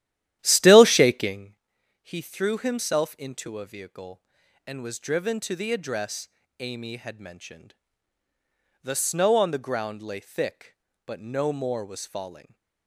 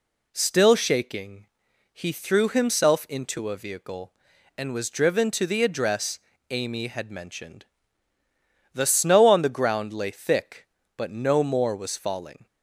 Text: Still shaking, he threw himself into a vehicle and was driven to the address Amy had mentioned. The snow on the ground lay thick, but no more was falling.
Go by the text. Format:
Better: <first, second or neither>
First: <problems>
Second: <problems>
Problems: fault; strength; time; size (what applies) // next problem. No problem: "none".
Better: second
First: starts louder than the rest; strong; until 1.5 s; 12.5 dB // pauses between "address" and "Amy"; slight; at 6.2 s; 0.30 s long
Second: pauses between "address" and "Amy"; slight; at 6.1 s; 0.30 s long